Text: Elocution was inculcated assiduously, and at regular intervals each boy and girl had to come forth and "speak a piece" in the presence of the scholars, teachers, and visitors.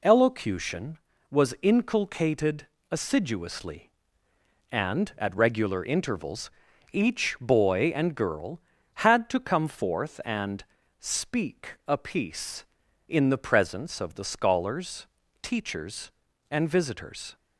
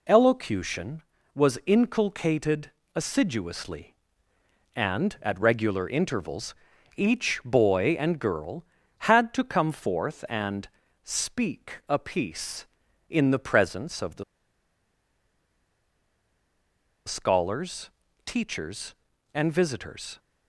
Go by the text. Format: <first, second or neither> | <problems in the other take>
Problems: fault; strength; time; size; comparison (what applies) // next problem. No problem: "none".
first | pauses between "inculcated" and "assiduously"; slight; at 2.7 s; 0.24 s long; slight in the first // pauses between "intervals" and "each"; at 6.5 s; 0.40 s long; also in the first // pauses between "and" and "speak"; slight; at 10.6 s; 0.36 s long; slight in the first // pauses between "the" and "scholars"; strong; at 14.2 s; 2.8 s long